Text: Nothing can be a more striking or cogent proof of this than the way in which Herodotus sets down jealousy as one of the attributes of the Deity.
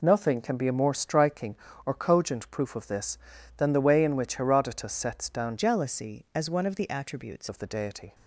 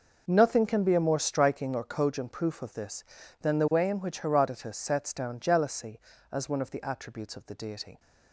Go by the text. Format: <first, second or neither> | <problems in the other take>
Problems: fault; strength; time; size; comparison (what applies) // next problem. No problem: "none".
second | changes voice from "jealousy" to "attributes"; from 5.5 to 7.4 s; 1.9 s long